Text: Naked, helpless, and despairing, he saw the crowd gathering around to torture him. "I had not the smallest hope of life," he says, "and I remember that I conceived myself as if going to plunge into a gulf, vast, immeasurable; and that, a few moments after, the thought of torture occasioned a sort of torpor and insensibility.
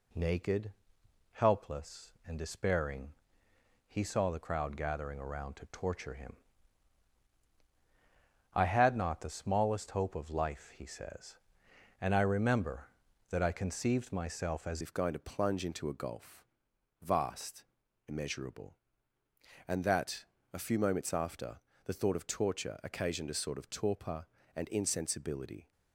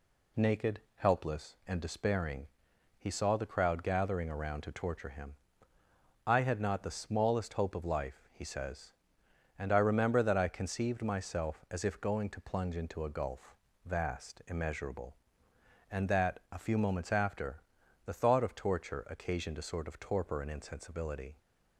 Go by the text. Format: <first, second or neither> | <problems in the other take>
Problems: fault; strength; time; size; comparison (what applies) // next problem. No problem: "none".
second | changes voice at "if"; from 14.8 s on; 10.9 s long